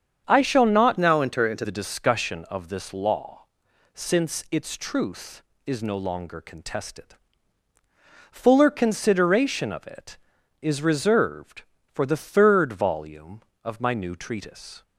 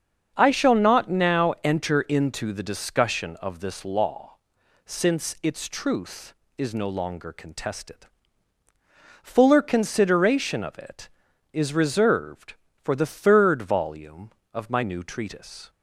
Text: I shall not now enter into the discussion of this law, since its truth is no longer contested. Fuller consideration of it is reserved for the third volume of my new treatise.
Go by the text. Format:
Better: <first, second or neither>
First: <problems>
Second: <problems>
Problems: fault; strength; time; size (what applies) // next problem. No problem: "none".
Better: second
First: starts louder than the rest; strong; until 1.2 s; 7.5 dB // changes voice from "now" to "into"; from 0.9 to 1.6 s; 0.7 s long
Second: starts louder than the rest; until 1.3 s; 6.5 dB